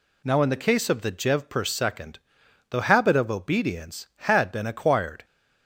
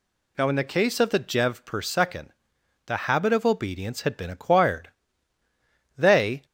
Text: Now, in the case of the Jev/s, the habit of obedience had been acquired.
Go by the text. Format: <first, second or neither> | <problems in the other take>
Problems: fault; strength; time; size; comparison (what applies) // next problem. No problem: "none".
first | goes on to say "They"; slight; from 5.9 s on; 0.48 s long